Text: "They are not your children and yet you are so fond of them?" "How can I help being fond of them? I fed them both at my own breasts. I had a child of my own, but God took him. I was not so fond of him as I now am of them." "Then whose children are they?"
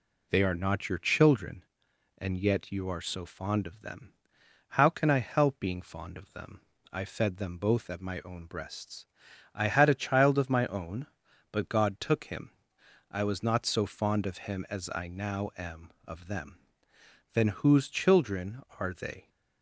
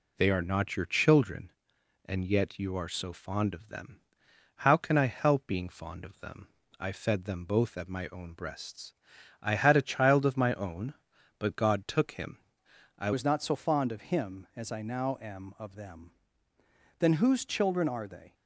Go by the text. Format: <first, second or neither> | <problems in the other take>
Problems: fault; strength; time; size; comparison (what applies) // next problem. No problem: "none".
first | changes voice at "was"; from 13.1 s on; 5.2 s long